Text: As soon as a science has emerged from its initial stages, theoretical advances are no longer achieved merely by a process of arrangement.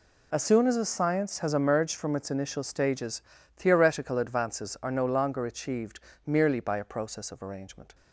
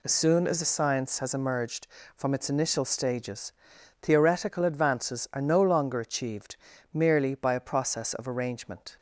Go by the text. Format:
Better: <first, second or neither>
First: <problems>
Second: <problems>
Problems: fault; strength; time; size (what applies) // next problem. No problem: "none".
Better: neither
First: pauses between "achieved" and "merely"; slight; at 5.9 s; 0.28 s long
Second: pauses between "achieved" and "merely"; at 6.5 s; 0.38 s long